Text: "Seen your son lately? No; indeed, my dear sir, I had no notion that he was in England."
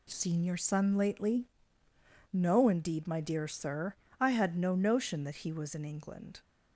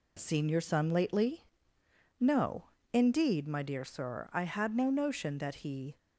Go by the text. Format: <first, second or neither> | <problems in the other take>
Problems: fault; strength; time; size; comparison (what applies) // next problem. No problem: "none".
first | stops before "was in England"; at 5.9 s